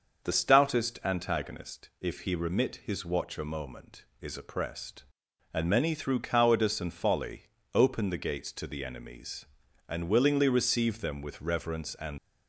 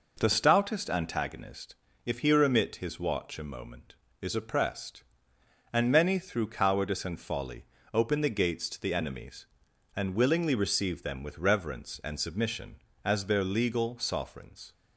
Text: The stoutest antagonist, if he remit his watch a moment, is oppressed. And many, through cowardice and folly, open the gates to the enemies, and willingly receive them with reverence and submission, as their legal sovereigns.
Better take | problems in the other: second | starts louder than the rest; until 1.2 s; 6 dB // stops before "submission as their legal sovereigns"; at 12.1 s

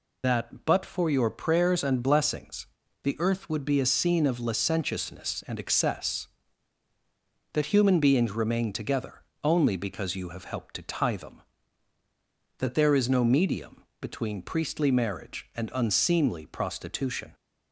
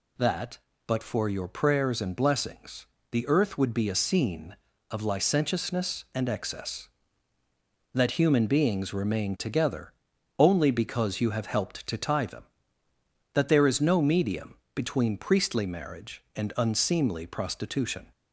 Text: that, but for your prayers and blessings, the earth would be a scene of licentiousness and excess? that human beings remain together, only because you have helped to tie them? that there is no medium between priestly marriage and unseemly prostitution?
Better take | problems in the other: second | loses the start of "that"; at 0.2 s; 75 ms // pauses between "medium" and "between"; slight; at 13.8 s; 0.16 s long; slight in the second

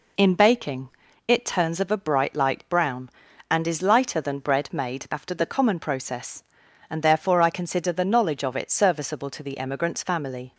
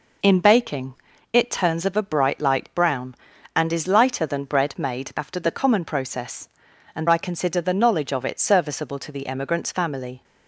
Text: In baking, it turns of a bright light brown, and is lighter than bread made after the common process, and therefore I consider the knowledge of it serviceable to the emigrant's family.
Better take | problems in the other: first | skips "therefore"; at 7.0 s

